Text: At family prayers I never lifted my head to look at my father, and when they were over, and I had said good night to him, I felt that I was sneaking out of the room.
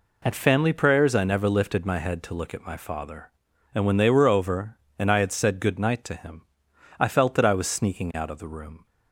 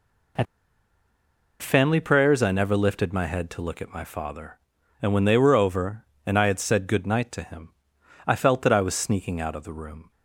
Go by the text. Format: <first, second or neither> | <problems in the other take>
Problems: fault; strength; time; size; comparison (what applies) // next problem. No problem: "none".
first | pauses between "At" and "family"; at 0.4 s; 1.1 s long